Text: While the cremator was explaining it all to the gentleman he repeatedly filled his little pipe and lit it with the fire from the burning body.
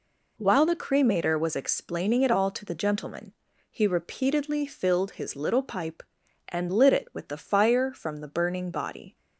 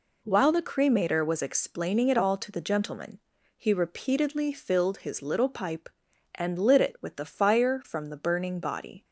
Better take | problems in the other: neither | pauses between "gentleman" and "he"; the same in both

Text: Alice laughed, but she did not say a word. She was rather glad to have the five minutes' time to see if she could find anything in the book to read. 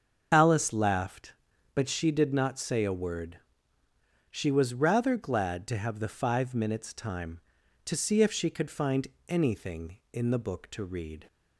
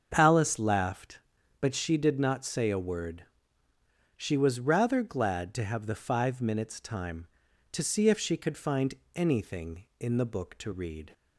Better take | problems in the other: second | loses the start of "Alice"; at 0.3 s; 65 ms // starts louder than the rest; until 1.3 s; 7 dB; also in the second // pauses between "find" and "anything"; slight; at 9.0 s; 0.22 s long; slight in the second

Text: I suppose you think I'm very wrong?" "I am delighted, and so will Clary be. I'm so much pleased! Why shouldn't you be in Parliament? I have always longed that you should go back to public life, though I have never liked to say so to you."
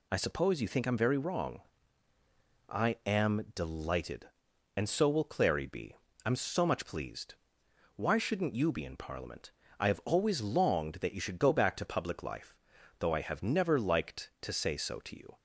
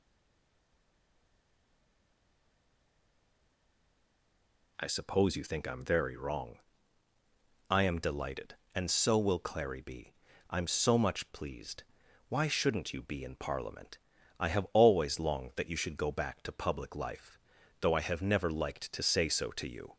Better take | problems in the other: first | stays silent before the first word; strong; until 4.7 s; 4.7 s long

